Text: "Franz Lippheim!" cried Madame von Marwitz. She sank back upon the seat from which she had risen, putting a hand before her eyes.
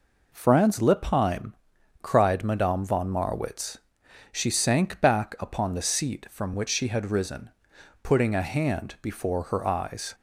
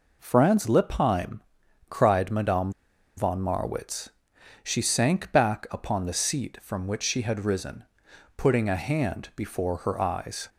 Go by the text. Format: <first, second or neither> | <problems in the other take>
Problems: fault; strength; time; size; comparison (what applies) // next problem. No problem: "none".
first | pauses between "Madame" and "von"; noticeable; at 2.7 s; 0.46 s long